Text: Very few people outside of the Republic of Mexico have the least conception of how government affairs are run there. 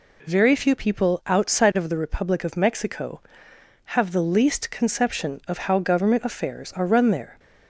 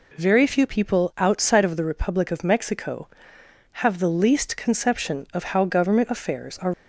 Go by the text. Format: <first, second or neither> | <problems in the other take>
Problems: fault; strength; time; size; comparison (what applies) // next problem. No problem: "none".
first | stops before "run there"; at 6.7 s